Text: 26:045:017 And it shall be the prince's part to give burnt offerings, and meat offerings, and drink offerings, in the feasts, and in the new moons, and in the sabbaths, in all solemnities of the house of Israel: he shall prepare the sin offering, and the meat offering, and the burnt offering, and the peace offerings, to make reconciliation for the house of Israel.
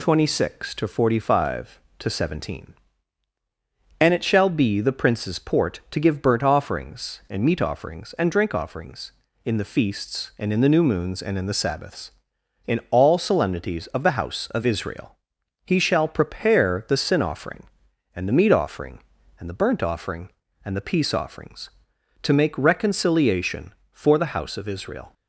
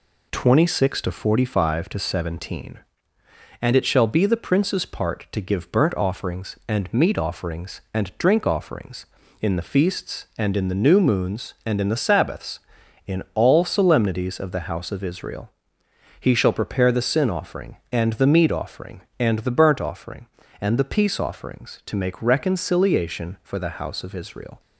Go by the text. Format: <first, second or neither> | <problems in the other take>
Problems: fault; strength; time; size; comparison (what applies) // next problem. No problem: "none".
second | says "port" for "part"; at 5.3 s